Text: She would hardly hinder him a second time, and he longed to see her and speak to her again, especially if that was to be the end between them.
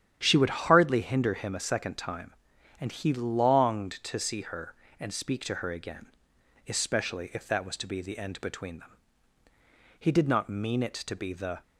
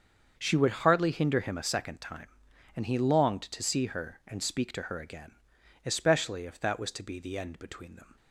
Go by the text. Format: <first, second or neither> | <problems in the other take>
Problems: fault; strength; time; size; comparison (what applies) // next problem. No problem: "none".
second | starts louder than the rest; strong; until 1.2 s; 10 dB; also in the second // goes on to say "He did not mean it to be the"; from 9.9 s on; 1.6 s long